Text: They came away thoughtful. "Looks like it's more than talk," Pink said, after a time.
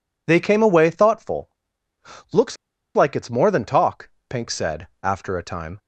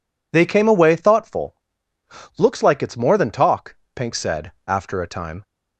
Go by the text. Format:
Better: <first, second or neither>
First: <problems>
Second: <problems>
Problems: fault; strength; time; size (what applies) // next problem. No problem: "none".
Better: second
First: pauses between "Looks" and "like"; at 2.5 s; 0.40 s long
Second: none